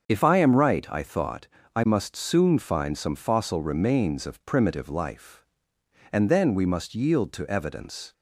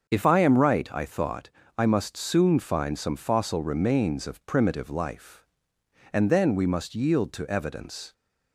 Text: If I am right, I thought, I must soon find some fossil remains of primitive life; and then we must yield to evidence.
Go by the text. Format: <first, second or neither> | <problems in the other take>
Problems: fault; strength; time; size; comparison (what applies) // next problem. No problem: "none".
neither | starts louder than the rest; the same in both